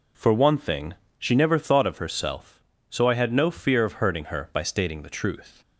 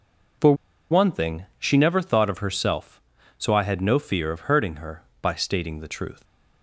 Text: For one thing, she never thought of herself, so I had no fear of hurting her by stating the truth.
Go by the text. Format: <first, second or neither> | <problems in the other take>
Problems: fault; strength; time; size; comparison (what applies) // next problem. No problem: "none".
first | pauses between "For" and "one"; slight; at 0.5 s; 0.35 s long